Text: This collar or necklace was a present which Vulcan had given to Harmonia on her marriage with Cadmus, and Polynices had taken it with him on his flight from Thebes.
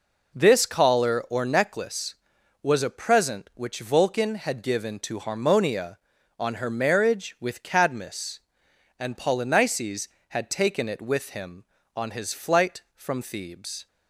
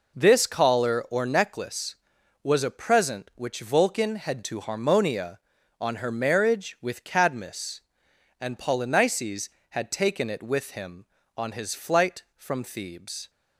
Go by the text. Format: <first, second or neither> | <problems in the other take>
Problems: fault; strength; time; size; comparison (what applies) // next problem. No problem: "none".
first | skips "given"; at 4.4 s